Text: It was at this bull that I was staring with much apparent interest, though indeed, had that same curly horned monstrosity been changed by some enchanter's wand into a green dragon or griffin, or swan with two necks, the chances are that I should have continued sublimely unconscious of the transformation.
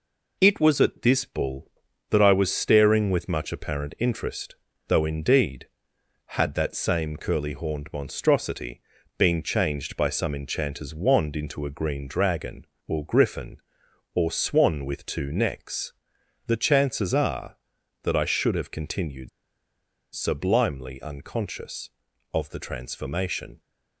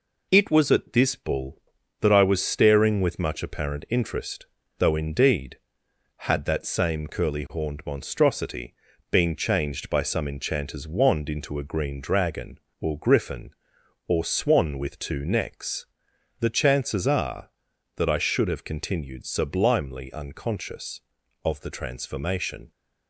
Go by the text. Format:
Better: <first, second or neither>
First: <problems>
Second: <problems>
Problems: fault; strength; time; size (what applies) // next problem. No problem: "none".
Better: second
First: pauses between "monstrosity" and "been"; slight; at 8.8 s; 0.36 s long // pauses between "continued" and "sublimely"; noticeable; at 19.2 s; 0.83 s long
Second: pauses between "monstrosity" and "been"; slight; at 8.7 s; 0.36 s long